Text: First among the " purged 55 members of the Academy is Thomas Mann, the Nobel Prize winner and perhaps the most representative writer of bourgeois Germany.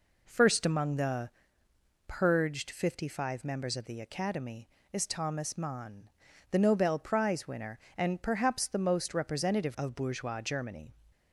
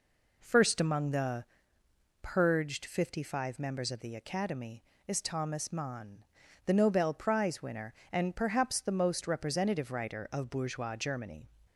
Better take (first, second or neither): second